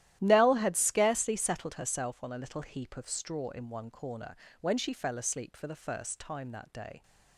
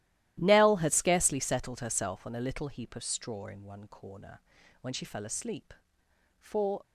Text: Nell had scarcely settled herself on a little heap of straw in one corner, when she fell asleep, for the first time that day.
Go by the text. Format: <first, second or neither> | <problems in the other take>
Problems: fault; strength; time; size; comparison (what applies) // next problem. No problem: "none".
first | starts louder than the rest; strong; until 1.4 s; 14 dB; strong in the first // stops before "the first time that day"; at 6.8 s